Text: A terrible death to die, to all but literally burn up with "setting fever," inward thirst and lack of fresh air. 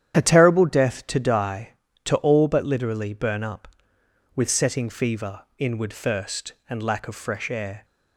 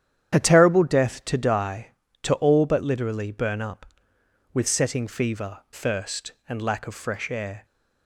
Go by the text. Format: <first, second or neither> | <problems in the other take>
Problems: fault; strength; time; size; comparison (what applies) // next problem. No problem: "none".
first | starts louder than the rest; strong; until 1.3 s; 9.5 dB; strong in the first // skips "inward"; at 5.6 s